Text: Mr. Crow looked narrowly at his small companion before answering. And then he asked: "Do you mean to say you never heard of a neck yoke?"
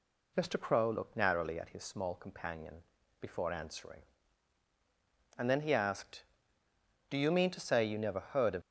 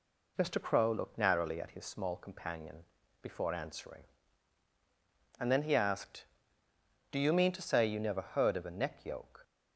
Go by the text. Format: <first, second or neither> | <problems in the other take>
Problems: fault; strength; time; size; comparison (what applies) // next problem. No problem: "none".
second | pauses between "companion" and "before"; at 2.7 s; 0.44 s long; also in the second // stops before "a neck yoke"; at 8.6 s